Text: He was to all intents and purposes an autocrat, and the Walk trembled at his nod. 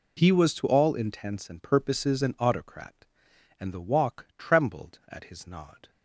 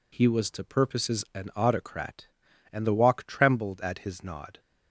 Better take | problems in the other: first | skips "all intents and"; at 0.6 s

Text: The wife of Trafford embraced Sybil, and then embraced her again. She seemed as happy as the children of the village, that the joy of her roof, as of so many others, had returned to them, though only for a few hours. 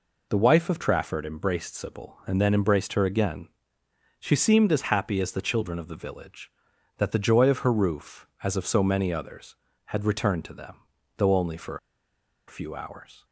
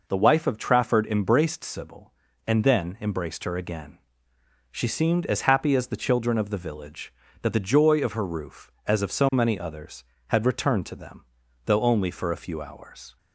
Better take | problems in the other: second | pauses between "for" and "a"; noticeable; at 11.7 s; 0.71 s long

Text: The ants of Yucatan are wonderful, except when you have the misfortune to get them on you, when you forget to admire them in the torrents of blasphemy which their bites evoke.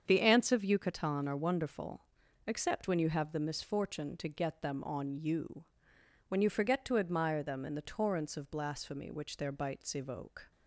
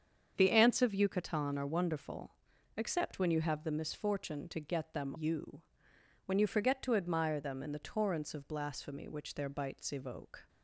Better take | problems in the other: first | starts louder than the rest; strong; until 1.3 s; 7.5 dB; strong in the first // skips "on"; at 5.1 s

